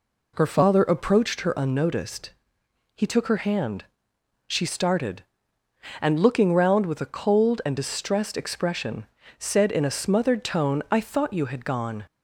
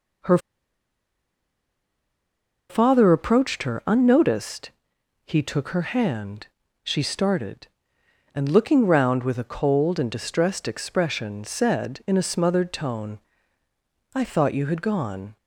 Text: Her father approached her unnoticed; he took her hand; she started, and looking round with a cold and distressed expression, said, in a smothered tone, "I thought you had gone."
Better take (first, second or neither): first